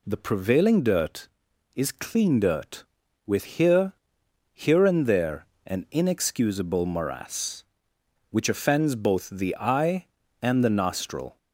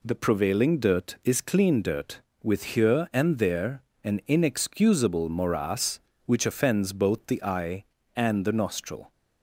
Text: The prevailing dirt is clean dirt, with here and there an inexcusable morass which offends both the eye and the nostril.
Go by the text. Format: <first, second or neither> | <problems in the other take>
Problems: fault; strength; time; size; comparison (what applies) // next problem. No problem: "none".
second | says "here" twice; at 4.5 s // pauses between "there" and "an"; slight; at 5.4 s; 0.22 s long; slight in the second